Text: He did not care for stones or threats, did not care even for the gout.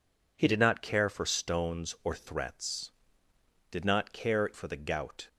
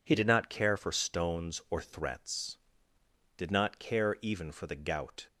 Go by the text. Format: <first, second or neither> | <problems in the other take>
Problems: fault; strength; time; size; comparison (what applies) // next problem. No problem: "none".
second | skips "even"; at 4.5 s